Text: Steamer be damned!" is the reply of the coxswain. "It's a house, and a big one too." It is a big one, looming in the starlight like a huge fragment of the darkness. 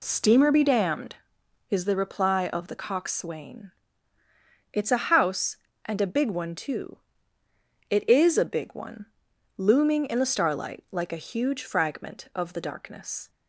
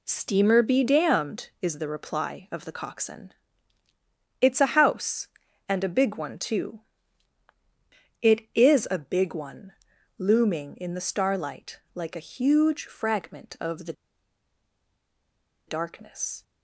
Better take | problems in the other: first | pauses between "the" and "darkness"; strong; at 13.9 s; 1.7 s long

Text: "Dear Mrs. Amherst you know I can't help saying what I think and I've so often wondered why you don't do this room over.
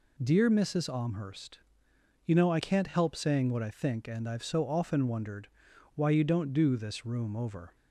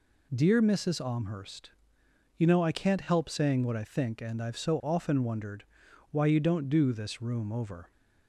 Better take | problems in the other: neither | pauses between "Amherst" and "you"; noticeable; the same in both // pauses between "wondered" and "why"; noticeable; the same in both

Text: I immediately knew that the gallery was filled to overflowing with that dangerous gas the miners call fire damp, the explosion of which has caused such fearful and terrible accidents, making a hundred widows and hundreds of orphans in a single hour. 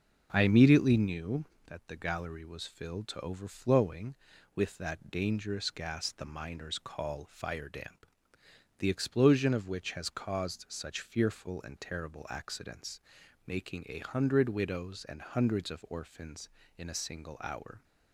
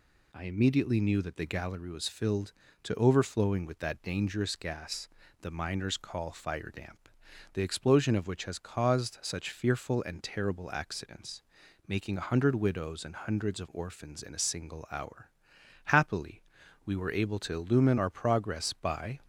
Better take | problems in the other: first | pauses between "gas" and "the"; slight; at 5.0 s; 0.34 s long // goes on to say "Happily we were able to illumine our progress by"; strong; from 15.8 s on; 3.3 s long

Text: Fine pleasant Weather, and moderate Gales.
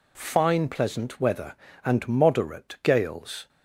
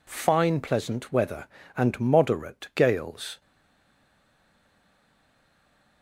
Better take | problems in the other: first | stays silent after the last word; strong; from 3.4 s on; 2.6 s long

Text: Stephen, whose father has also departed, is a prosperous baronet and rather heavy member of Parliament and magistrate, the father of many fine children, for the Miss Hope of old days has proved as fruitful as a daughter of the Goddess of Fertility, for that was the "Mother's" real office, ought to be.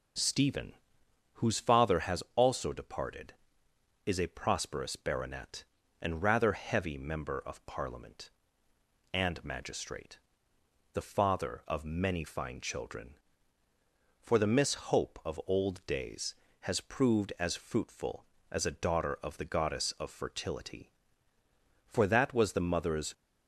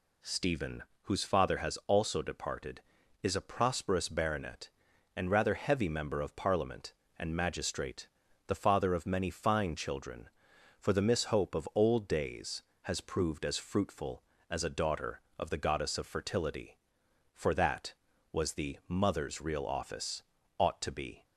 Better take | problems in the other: second | pauses between "Miss" and "Hope"; slight; at 14.7 s; 0.16 s long // stops before "real office ought to be"; at 23.1 s

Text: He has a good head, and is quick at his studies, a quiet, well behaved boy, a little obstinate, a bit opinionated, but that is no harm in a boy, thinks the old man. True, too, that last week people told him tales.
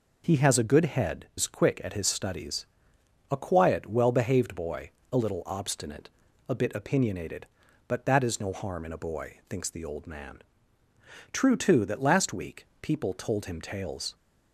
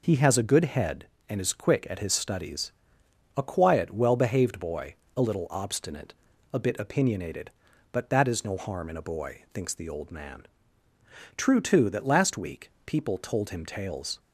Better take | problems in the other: second | skips "and"; at 1.3 s // pauses between "week" and "people"; slight; at 12.6 s; 0.16 s long; slight in the second

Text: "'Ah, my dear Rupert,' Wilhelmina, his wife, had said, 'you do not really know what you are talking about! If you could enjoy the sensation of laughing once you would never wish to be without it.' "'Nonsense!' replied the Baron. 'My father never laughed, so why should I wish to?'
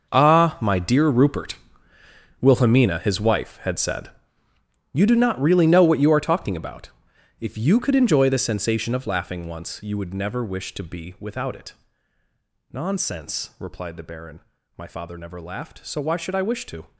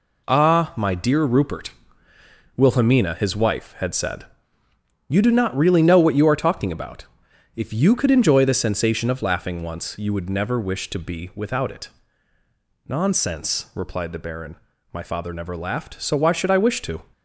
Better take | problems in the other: second | gets quieter; strong; throughout; 13.5 dB

